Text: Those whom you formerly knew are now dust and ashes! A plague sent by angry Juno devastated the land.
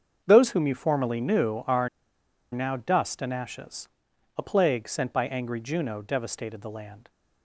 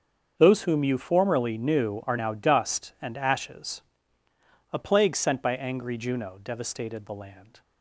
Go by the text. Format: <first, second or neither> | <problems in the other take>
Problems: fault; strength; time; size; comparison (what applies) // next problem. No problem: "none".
second | starts louder than the rest; strong; until 1.2 s; 7 dB; also in the second // pauses between "are" and "now"; noticeable; at 1.8 s; 0.63 s long